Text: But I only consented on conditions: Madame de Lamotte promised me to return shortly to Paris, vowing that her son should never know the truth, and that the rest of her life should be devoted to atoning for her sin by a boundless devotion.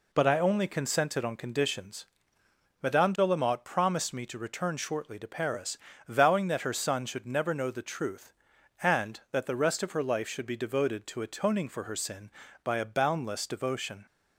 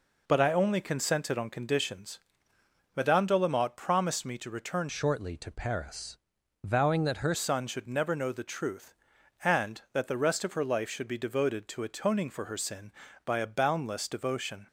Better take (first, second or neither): first